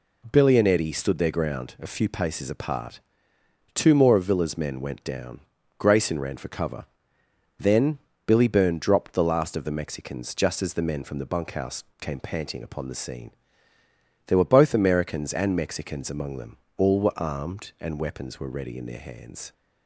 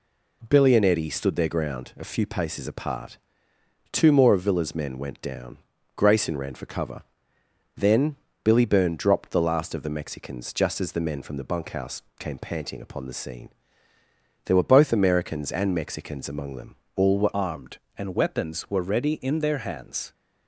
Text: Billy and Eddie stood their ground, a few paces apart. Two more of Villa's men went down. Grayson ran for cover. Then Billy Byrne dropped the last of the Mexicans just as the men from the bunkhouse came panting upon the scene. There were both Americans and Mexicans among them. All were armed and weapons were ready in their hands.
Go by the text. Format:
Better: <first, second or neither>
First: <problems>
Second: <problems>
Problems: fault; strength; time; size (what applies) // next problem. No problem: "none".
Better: first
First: pauses between "Then" and "Billy"; slight; at 7.9 s; 0.28 s long // pauses between "bunkhouse" and "came"; slight; at 11.8 s; 0.18 s long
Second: pauses between "Then" and "Billy"; slight; at 8.1 s; 0.28 s long // pauses between "bunkhouse" and "came"; slight; at 12.0 s; 0.18 s long // changes voice at "armed"; from 17.3 s on; 2.8 s long